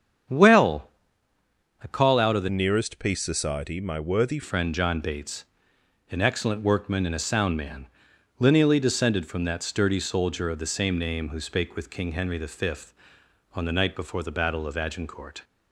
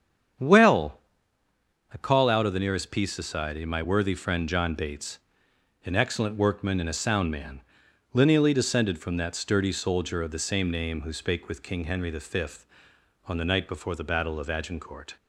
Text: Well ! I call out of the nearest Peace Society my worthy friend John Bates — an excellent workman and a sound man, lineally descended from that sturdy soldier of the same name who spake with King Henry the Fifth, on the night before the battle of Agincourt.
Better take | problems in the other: second | starts louder than the rest; strong; until 2.2 s; 8 dB; strong in the second // changes voice from "nearest" to "worthy"; from 2.4 to 4.3 s; 1.9 s long

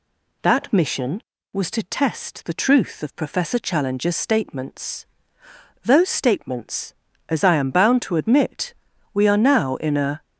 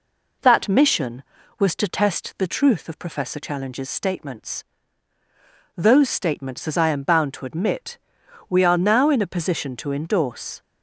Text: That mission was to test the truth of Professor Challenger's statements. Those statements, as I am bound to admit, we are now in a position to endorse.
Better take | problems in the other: second | stops before "position to endorse"; at 10.2 s

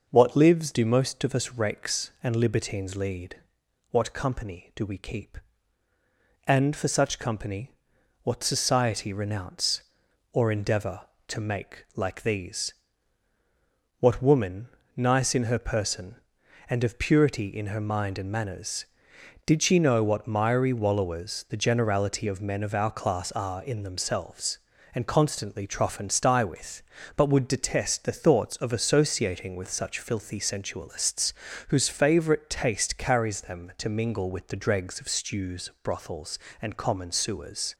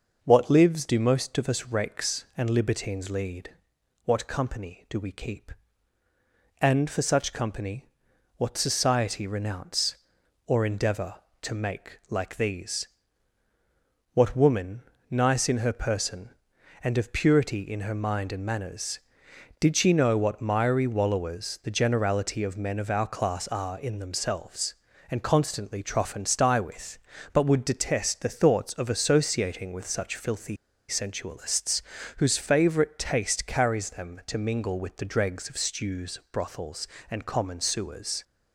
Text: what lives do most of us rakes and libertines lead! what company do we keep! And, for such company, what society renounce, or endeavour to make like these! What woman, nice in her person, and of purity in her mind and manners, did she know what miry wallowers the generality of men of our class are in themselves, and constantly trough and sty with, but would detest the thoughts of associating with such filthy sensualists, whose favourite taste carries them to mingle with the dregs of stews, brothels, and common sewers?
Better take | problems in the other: first | pauses between "filthy" and "sensualists"; slight; at 30.5 s; 0.33 s long

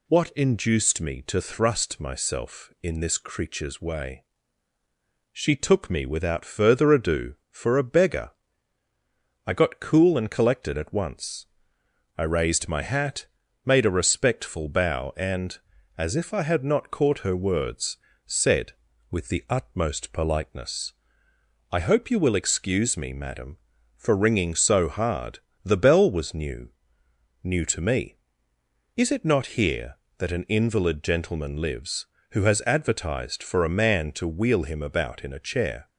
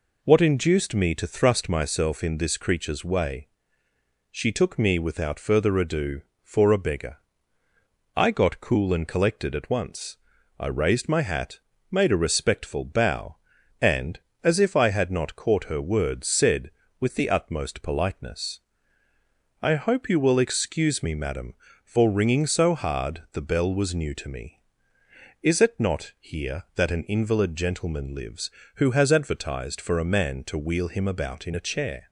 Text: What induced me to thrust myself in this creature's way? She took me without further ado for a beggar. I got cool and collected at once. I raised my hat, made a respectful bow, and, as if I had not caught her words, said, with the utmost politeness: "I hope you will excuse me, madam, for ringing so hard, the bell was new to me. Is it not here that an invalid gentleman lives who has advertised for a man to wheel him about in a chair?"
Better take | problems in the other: second | says "new" twice; at 27.4 s

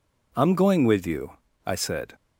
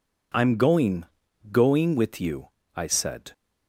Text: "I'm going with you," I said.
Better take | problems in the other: first | says "going" twice; at 1.5 s

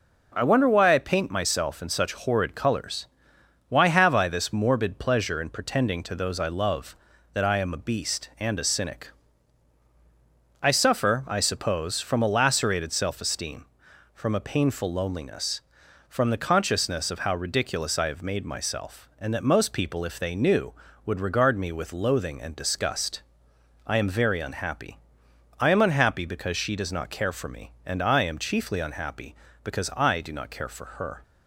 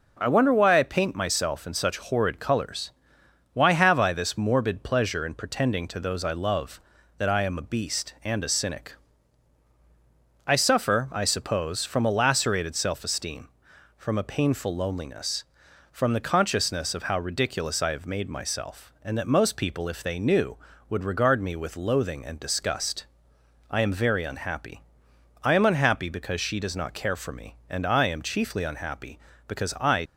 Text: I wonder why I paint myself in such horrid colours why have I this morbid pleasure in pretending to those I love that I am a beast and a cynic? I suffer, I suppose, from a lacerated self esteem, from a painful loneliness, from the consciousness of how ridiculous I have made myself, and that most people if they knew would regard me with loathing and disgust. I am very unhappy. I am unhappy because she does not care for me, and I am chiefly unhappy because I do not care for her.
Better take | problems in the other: first | pauses between "colours" and "why"; noticeable; at 2.9 s; 0.62 s long; noticeable in the first // stops before "do not care for her"; at 30.0 s

